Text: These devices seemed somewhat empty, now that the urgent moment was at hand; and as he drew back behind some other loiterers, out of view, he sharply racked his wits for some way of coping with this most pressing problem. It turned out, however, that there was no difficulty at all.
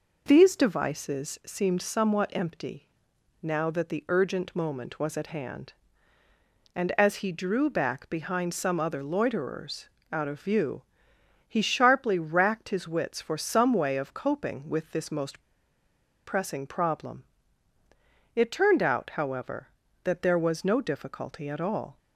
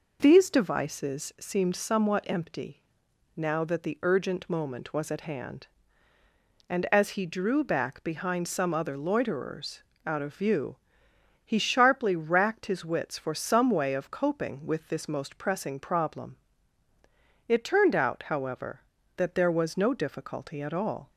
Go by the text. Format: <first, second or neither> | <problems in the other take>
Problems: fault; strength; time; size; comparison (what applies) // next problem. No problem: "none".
second | pauses between "most" and "pressing"; noticeable; at 15.3 s; 0.86 s long